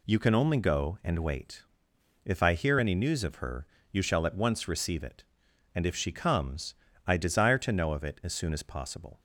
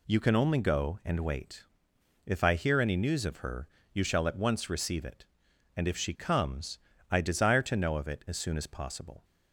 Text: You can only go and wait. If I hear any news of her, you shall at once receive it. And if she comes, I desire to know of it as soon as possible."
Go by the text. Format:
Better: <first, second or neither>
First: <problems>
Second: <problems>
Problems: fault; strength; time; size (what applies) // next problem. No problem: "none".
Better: neither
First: none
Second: none